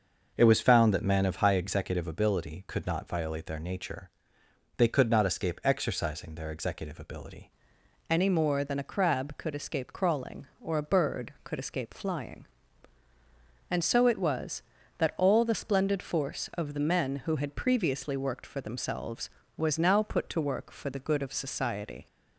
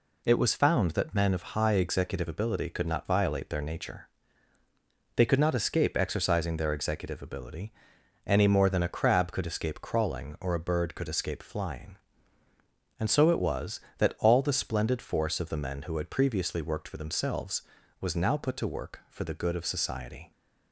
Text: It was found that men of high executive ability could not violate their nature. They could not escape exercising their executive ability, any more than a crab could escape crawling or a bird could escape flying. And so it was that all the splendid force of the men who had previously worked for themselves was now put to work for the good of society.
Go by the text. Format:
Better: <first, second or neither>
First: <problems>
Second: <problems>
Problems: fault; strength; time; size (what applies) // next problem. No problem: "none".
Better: second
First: starts louder than the rest; noticeable; until 1.3 s; 6 dB // changes voice at "any"; from 8.0 s on; 14.0 s long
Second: none